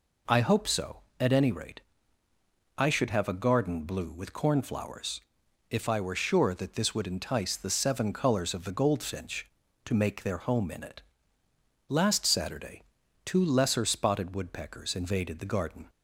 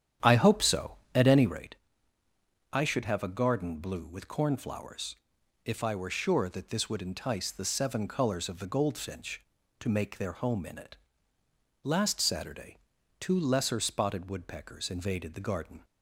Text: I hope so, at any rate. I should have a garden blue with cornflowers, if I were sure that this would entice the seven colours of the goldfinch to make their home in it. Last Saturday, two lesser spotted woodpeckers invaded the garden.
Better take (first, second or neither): first